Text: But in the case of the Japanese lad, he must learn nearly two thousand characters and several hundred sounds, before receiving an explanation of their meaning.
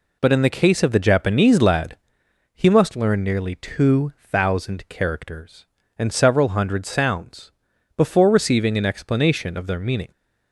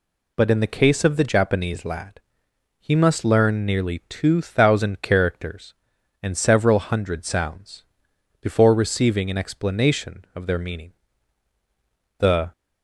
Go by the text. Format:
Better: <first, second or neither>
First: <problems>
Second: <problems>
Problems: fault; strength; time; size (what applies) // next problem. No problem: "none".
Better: first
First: none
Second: goes on to say "The"; slight; from 12.1 s on; 0.32 s long